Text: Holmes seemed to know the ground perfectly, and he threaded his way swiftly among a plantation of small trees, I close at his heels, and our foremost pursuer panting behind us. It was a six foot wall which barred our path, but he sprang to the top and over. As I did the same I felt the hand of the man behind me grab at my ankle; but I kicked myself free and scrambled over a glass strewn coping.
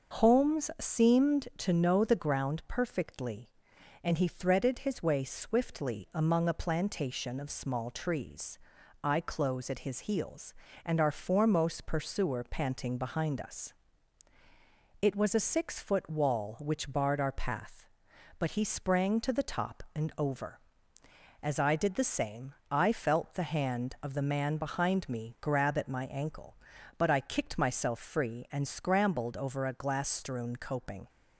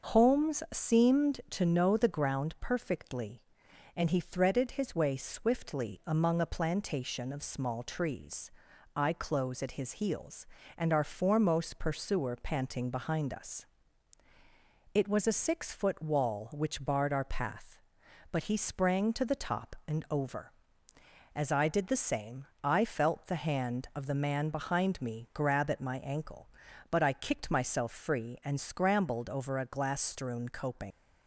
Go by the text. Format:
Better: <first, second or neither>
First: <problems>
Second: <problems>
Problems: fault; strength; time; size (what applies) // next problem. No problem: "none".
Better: first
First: starts louder than the rest; until 1.2 s; 6 dB // pauses between "same" and "I"; slight; at 22.5 s; 0.18 s long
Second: starts louder than the rest; until 1.1 s; 6 dB // pauses between "same" and "I"; slight; at 22.4 s; 0.18 s long // leaves "coping" unfinished; at 30.9 s; 100 ms